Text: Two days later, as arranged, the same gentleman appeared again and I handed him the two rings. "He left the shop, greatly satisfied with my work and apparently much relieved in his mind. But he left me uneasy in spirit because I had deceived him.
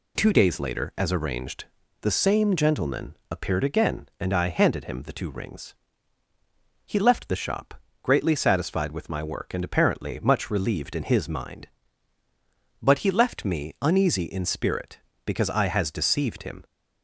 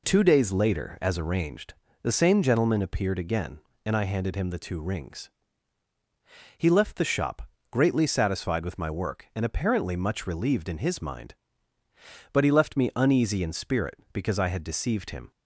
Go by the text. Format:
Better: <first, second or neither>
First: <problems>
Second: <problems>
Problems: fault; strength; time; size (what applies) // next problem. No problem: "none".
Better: second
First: says "has" for "had"; at 15.6 s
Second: none